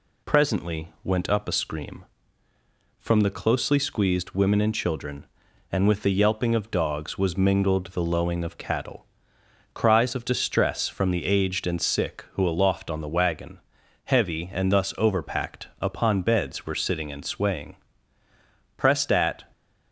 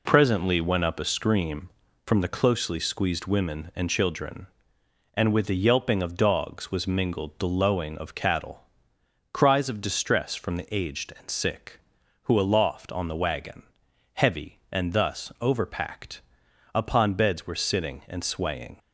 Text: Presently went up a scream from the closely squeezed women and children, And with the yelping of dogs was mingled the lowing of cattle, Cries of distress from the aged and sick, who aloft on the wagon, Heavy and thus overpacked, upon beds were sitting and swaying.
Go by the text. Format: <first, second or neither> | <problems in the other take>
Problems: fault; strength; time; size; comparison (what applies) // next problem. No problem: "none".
second | goes on to say "Pressed at"; noticeable; from 18.7 s on; 0.66 s long